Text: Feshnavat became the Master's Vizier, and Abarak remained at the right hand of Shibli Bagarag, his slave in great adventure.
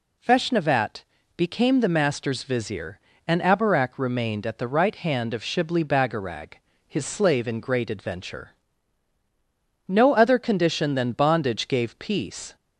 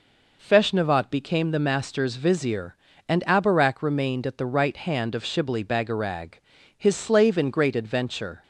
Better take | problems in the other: second | pauses between "Feshnavat" and "became"; slight; at 1.0 s; 0.32 s long // goes on to say "No other condition than bondage gave peace"; strong; from 9.8 s on; 2.6 s long

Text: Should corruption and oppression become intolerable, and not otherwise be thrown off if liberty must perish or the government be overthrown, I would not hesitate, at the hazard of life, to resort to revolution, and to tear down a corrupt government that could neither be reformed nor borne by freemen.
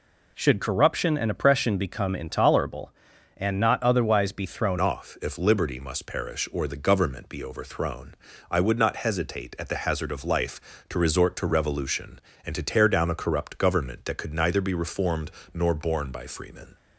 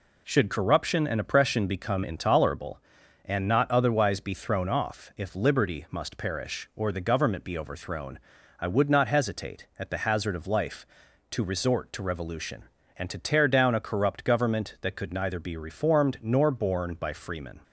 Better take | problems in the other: second | changes voice at "off"; from 4.7 s on; 12.0 s long // pauses between "reformed" and "nor"; slight; at 15.3 s; 0.24 s long

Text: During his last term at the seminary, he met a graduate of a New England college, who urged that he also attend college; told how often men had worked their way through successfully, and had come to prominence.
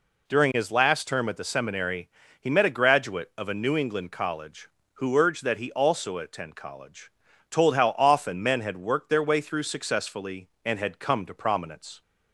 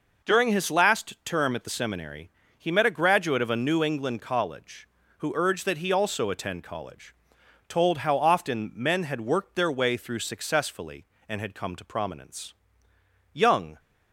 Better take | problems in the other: first | goes on to say "Young"; slight; from 13.3 s on; 0.46 s long

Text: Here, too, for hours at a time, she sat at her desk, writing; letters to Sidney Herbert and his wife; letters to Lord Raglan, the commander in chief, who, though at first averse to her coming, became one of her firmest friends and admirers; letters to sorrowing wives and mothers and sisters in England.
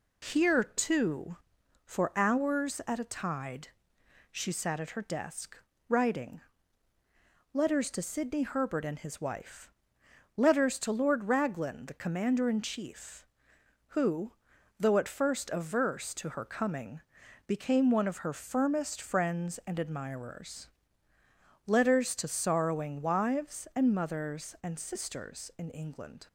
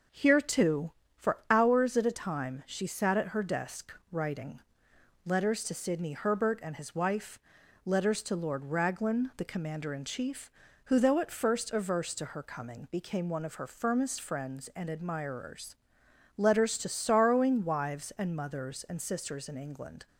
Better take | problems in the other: second | says "tide" for "time"; at 3.0 s

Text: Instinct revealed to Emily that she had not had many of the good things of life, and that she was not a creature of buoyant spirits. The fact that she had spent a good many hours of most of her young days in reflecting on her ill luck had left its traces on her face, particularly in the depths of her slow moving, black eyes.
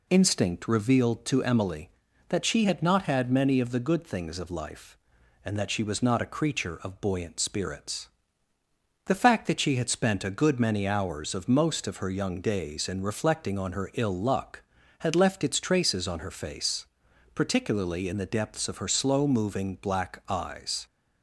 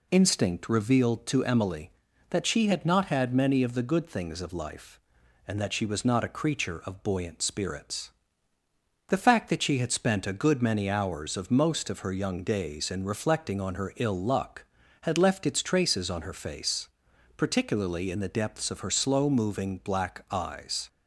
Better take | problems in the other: neither | none

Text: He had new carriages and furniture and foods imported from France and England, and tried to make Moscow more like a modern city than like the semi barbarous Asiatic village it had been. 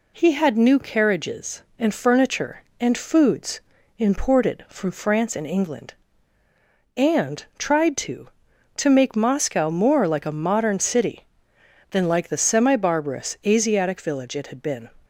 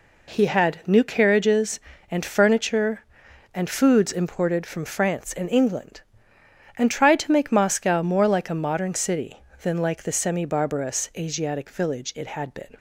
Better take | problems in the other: second | pauses between "foods" and "imported"; slight; at 3.6 s; 0.36 s long // says "to" twice; at 8.7 s

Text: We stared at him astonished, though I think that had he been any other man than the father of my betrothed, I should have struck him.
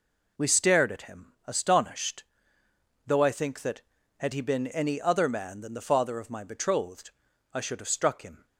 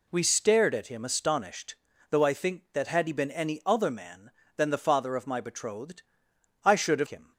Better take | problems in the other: first | skips "struck"; at 7.0 s

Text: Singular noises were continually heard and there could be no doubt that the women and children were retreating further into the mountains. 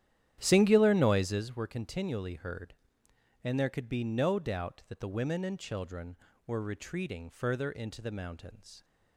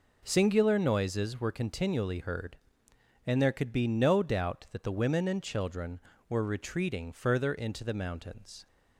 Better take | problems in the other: second | starts louder than the rest; strong; until 1.6 s; 11 dB

